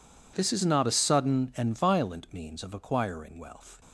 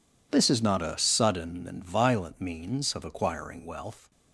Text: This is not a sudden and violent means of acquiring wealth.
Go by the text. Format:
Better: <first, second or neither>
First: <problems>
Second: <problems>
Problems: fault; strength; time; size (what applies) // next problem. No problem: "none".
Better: neither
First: none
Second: none